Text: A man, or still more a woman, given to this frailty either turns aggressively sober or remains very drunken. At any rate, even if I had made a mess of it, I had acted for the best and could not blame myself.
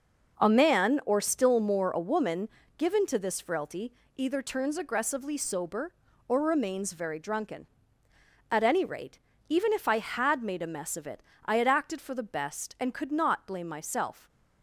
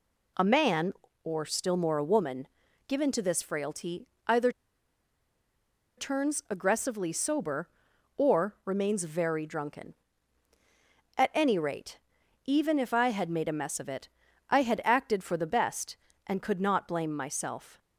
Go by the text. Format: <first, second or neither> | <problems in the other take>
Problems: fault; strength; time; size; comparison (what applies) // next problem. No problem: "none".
first | pauses between "frailty" and "either"; slight; at 4.0 s; 0.18 s long; slight in the first // pauses between "either" and "turns"; strong; at 4.4 s; 1.4 s long